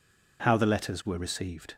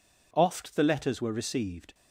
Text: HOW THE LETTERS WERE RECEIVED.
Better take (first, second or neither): first